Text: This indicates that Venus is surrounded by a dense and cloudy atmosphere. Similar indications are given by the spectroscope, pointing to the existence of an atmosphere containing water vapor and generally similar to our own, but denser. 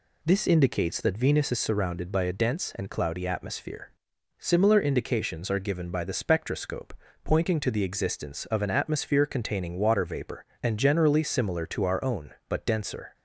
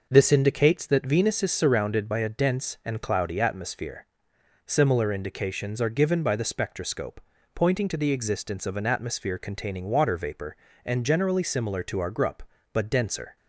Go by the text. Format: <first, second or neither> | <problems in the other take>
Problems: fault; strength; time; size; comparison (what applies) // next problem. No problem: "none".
first | says "grup" for "own"; at 12.0 s